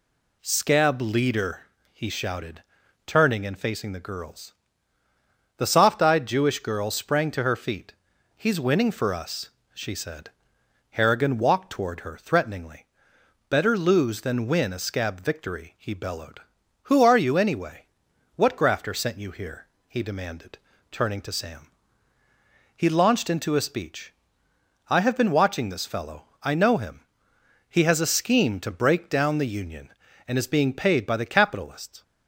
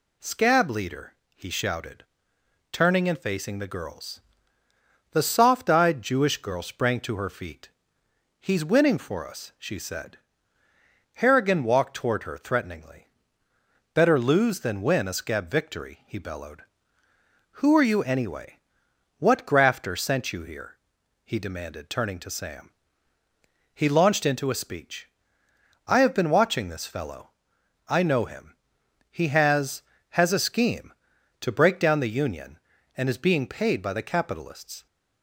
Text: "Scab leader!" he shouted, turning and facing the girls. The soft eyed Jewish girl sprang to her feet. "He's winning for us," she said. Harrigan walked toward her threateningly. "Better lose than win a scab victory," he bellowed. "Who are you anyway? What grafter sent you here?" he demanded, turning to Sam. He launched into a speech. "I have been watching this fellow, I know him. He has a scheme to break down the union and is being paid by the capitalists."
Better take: first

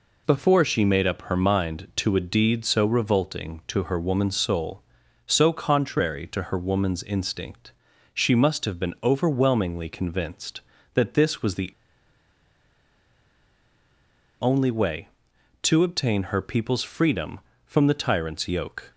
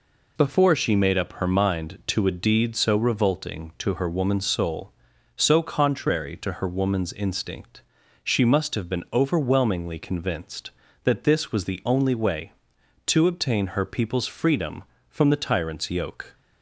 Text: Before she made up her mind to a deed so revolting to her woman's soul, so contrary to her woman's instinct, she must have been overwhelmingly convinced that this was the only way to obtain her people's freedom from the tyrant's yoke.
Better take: second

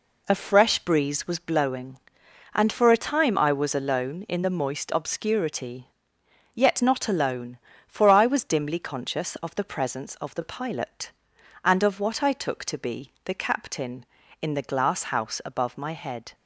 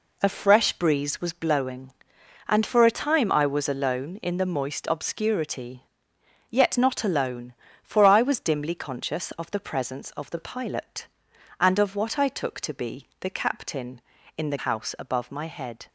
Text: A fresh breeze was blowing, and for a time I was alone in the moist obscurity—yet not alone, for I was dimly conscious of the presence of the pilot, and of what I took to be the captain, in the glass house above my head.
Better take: first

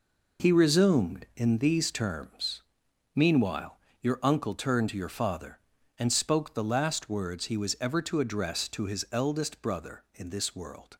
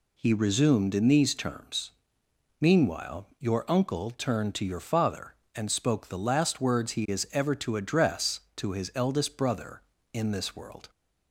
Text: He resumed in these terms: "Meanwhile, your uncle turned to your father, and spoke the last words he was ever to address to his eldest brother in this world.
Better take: first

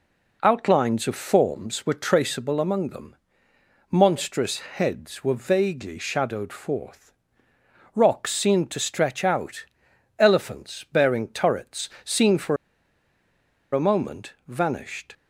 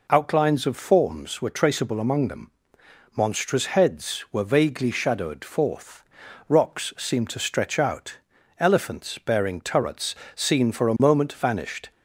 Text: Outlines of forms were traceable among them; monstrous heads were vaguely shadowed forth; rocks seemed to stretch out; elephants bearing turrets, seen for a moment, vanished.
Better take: second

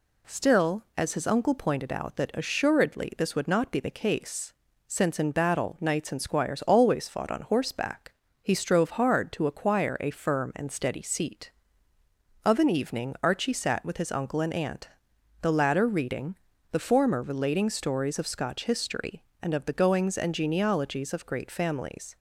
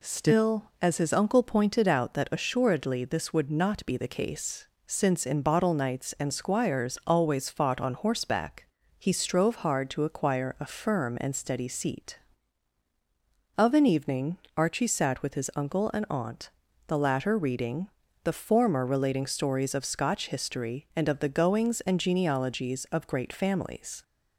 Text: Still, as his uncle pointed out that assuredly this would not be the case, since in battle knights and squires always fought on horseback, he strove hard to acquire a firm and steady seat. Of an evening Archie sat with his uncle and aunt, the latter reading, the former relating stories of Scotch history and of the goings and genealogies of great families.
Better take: first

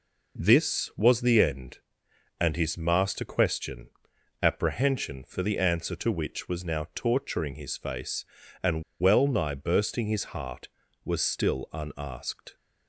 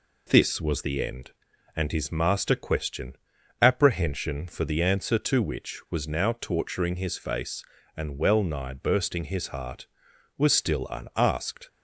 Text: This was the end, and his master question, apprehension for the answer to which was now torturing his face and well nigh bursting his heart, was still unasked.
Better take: second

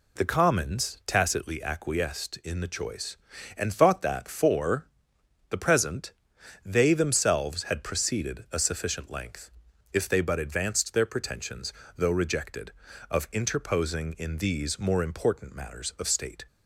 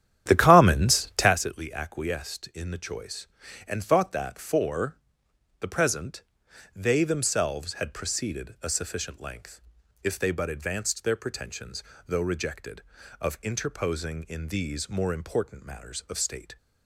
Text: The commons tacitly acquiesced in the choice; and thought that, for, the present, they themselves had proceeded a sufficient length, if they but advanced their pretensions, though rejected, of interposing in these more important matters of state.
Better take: first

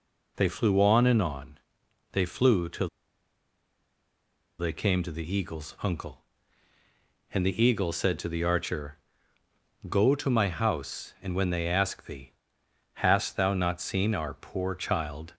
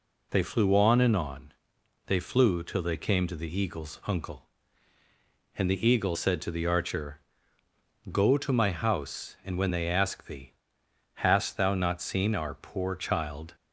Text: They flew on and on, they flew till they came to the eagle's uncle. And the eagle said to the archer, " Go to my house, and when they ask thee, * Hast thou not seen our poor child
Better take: second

